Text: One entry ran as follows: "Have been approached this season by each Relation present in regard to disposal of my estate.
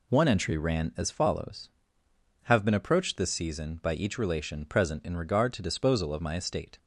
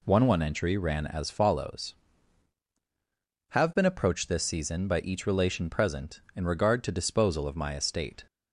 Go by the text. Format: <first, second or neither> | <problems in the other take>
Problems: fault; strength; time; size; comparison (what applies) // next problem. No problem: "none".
first | says "One" twice; at 0.2 s